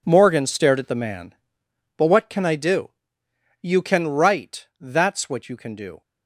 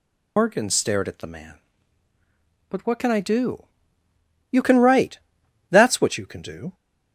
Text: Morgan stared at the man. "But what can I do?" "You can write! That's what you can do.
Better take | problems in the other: first | loses the start of "Morgan"; at 0.3 s; 90 ms

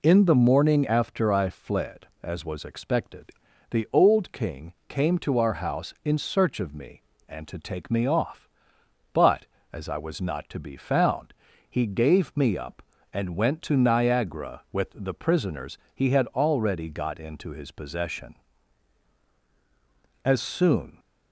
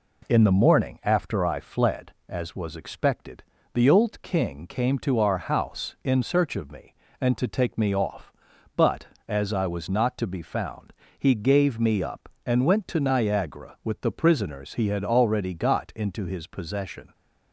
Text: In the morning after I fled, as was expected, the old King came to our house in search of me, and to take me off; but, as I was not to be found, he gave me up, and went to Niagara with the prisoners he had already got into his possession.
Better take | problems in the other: second | pauses between "King" and "came"; slight; at 4.7 s; 0.16 s long // pauses between "prisoners" and "he"; slight; at 15.7 s; 0.18 s long // goes on to say "As soon"; noticeable; from 20.2 s on; 0.74 s long

